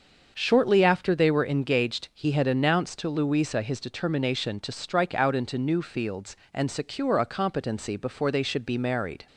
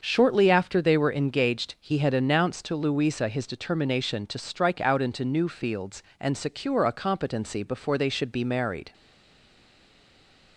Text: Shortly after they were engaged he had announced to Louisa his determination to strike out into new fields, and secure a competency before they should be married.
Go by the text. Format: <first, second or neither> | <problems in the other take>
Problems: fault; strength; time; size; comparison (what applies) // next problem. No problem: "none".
first | starts louder than the rest; until 1.0 s; 6.5 dB; also in the first // stays silent after the last word; noticeable; from 8.9 s on; 1.6 s long